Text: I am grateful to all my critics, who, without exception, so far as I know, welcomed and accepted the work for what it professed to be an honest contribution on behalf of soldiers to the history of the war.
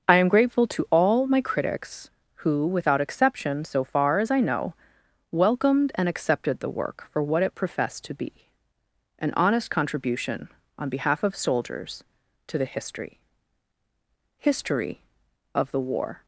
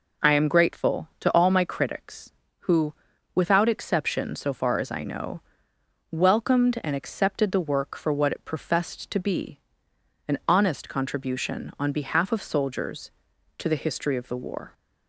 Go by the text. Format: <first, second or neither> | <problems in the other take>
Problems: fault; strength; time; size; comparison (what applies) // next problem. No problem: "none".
second | starts louder than the rest; until 1.1 s; 6 dB // pauses between "be" and "an"; noticeable; at 8.5 s; 0.68 s long; noticeable in the second // says "history" twice; at 14.3 s